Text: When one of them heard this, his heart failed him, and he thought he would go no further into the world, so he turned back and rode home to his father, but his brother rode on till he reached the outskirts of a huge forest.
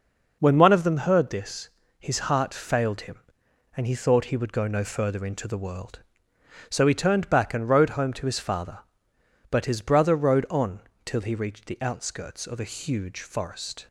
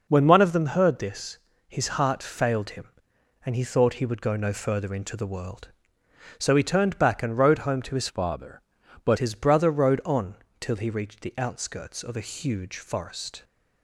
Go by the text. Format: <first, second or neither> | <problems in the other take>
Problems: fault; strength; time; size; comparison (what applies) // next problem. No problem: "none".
first | changes voice from "father" to "but"; from 8.0 to 9.1 s; 1.1 s long // pauses between "on" and "till"; slight; at 10.3 s; 0.26 s long; slight in the first